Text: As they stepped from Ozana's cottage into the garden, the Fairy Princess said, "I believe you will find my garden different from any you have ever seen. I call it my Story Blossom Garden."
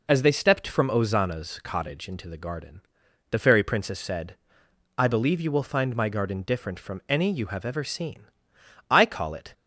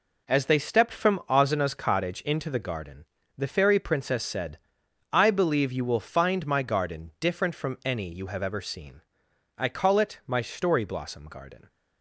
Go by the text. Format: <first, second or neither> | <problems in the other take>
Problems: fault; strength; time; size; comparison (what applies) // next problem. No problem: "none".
second | stops before "my Story Blossom Garden"; at 9.5 s